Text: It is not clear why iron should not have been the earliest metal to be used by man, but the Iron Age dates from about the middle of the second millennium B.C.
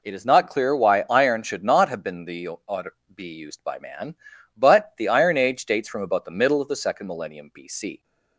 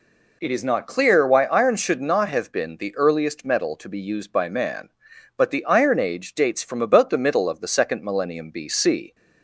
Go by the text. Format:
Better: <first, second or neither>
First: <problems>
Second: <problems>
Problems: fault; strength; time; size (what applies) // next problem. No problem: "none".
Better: second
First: skips "earliest metal to"; at 2.8 s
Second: none